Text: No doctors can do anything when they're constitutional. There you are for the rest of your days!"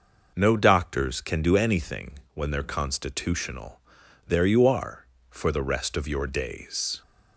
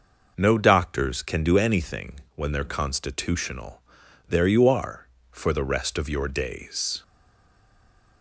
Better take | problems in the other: first | pauses between "anything" and "when"; slight; at 2.2 s; 0.16 s long; slight in the first // stays silent after the last word; noticeable; from 7.0 s on; 1.2 s long

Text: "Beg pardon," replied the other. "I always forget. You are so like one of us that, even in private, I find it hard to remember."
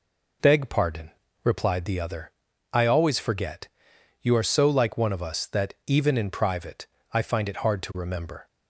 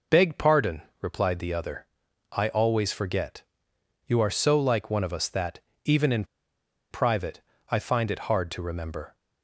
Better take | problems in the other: first | pauses between "in" and "private"; noticeable; at 6.2 s; 0.66 s long

